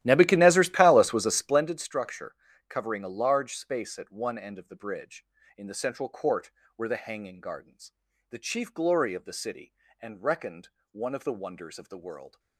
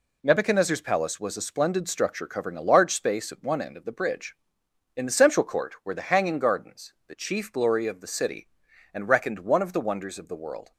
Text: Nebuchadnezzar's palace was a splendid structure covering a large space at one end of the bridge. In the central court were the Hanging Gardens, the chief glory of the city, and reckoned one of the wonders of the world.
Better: second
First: starts louder than the rest; strong; until 1.7 s; 14 dB // pauses between "structure" and "covering"; slight; at 2.3 s; 0.36 s long // pauses between "reckoned" and "one"; slight; at 10.6 s; 0.22 s long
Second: none

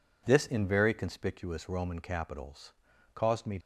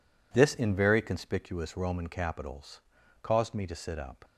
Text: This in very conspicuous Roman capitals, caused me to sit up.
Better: second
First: stops before "to sit up"; at 3.6 s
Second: none

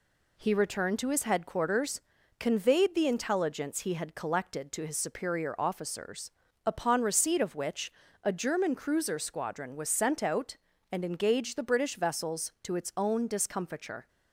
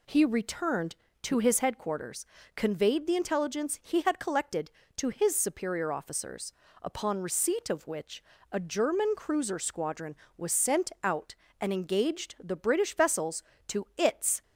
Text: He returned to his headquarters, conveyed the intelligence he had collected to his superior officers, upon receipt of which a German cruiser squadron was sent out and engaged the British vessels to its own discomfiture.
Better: first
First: pauses between "which" and "a"; slight; at 7.9 s; 0.30 s long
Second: pauses between "which" and "a"; slight; at 8.2 s; 0.30 s long // stops before "own discomfiture"; at 14.4 s

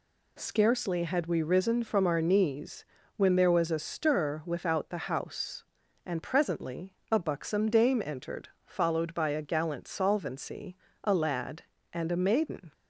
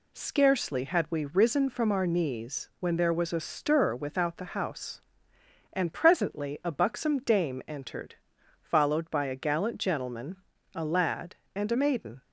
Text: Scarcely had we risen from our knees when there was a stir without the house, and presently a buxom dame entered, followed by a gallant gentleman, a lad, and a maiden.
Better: second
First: pauses between "knees" and "when"; slight; at 2.8 s; 0.30 s long // pauses between "presently" and "a"; slight; at 6.9 s; 0.18 s long // says "solvency" for "gentleman"; at 9.8 s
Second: none

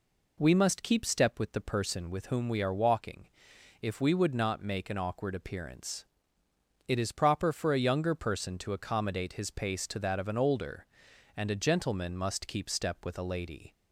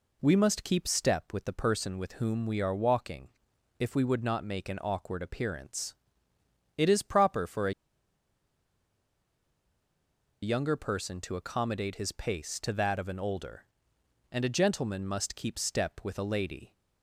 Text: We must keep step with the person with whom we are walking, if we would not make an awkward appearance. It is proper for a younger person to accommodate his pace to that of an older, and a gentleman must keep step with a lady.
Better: first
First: none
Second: pauses between "a" and "younger"; strong; at 7.7 s; 2.6 s long

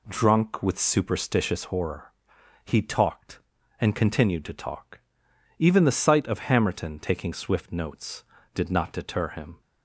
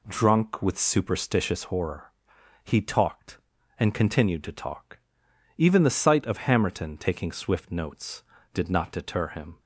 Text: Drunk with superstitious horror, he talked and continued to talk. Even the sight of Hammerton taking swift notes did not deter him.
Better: neither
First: none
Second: none

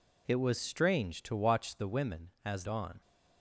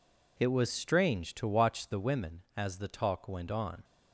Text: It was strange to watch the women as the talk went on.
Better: second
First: skips "the talk went"; at 2.6 s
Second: none

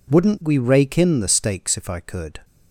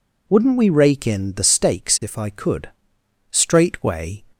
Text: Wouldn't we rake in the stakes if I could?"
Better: first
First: none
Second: goes on to say "Straightway"; noticeable; from 3.3 s on; 0.92 s long

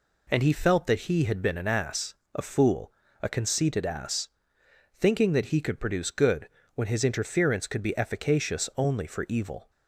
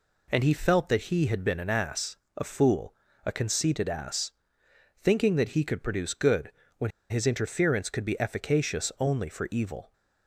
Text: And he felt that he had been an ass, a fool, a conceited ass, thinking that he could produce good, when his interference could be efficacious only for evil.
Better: first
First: none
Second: pauses between "when" and "his"; slight; at 6.9 s; 0.19 s long

